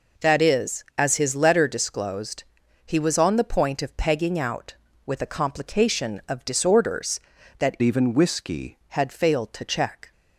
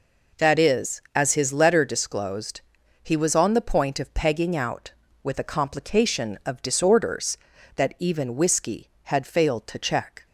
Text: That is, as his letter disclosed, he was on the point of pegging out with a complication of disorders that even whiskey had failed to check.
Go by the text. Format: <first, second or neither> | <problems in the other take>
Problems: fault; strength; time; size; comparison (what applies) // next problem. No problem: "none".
second | changes voice from "even" to "whiskey"; from 7.8 to 8.7 s; 0.9 s long